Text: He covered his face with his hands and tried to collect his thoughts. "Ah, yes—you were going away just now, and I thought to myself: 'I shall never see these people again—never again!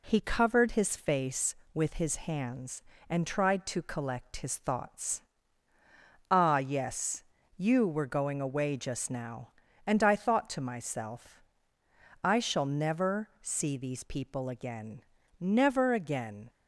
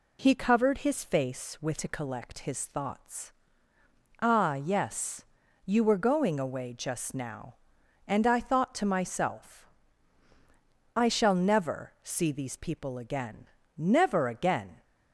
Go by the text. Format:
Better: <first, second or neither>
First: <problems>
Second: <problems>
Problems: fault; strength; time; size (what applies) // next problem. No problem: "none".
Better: first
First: none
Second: skips "his hands and tried"; at 1.7 s